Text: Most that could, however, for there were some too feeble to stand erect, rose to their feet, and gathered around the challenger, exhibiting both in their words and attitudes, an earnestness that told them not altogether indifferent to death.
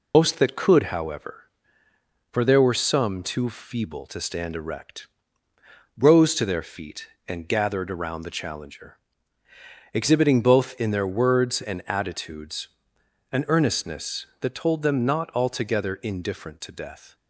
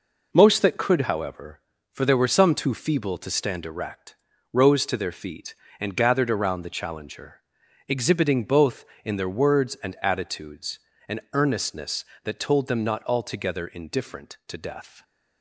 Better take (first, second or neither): second